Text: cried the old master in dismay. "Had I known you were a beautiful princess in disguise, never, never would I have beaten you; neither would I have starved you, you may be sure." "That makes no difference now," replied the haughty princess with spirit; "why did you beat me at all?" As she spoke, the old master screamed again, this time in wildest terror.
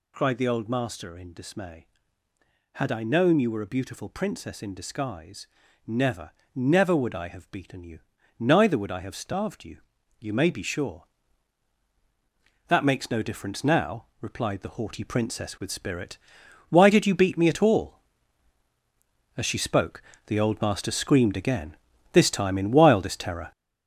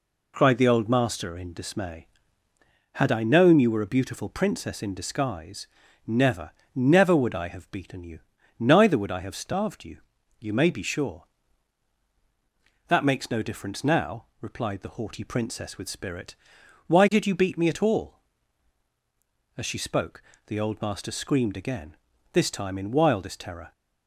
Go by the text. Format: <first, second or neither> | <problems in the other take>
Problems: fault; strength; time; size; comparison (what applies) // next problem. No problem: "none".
second | gets louder; throughout; 7 dB